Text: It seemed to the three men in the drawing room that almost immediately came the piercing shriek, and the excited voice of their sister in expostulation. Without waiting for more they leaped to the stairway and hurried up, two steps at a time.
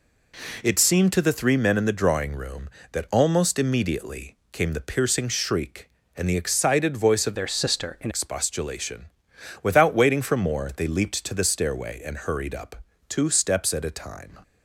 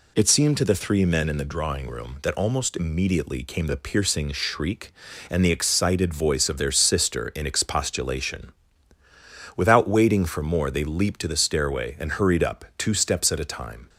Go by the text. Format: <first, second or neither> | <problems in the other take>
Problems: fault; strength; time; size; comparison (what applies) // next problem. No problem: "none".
second | pauses between "immediately" and "came"; slight; at 4.3 s; 0.16 s long // changes voice from "their" to "in"; from 7.3 to 8.1 s; 0.8 s long